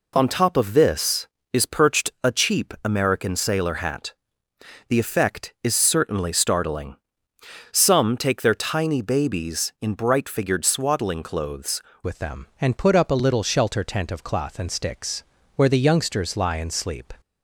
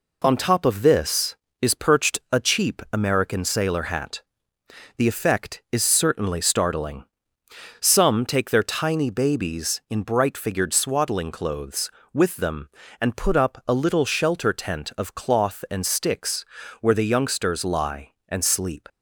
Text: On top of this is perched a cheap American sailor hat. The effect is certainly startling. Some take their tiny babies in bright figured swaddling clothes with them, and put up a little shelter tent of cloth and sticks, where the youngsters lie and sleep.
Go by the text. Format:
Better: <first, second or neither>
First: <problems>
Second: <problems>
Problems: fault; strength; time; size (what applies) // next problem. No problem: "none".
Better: second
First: changes voice at "with"; from 12.0 s on; 5.1 s long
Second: none